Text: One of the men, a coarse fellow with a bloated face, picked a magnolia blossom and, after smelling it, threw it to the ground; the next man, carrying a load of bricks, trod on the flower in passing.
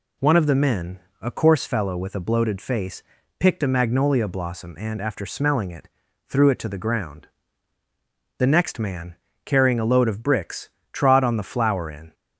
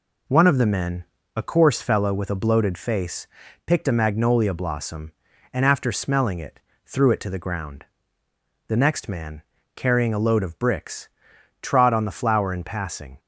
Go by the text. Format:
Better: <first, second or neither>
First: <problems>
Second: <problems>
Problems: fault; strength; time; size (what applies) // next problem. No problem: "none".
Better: second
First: stops before "passing"; at 12.1 s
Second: none